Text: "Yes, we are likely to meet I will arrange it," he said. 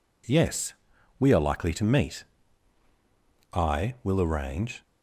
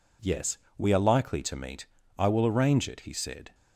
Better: second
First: pauses between "meet" and "I"; strong; at 2.2 s; 1.2 s long // stops before "it he said"; at 4.8 s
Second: pauses between "meet" and "I"; slight; at 1.8 s; 0.32 s long

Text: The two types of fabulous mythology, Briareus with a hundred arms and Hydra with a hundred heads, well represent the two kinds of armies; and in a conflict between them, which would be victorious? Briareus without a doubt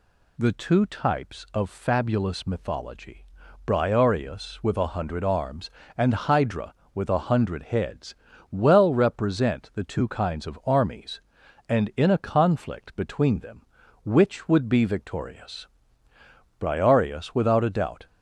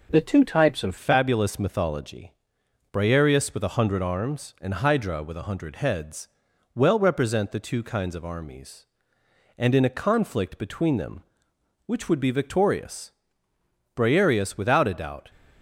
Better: first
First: none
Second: changes voice at "fabulous"; from 0.9 s on; 14.3 s long

